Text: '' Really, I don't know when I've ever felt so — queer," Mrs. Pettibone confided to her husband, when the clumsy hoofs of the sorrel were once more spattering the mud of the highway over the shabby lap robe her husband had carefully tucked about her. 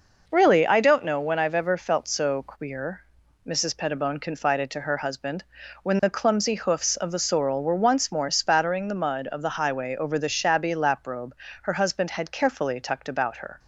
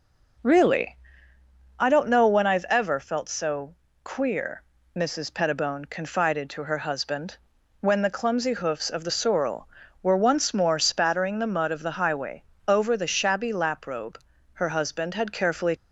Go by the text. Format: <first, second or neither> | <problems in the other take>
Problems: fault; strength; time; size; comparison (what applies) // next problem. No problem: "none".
first | pauses between "highway" and "over"; slight; at 12.4 s; 0.24 s long // pauses between "robe" and "her"; slight; at 14.1 s; 0.32 s long; slight in the first // stops before "tucked about her"; at 15.7 s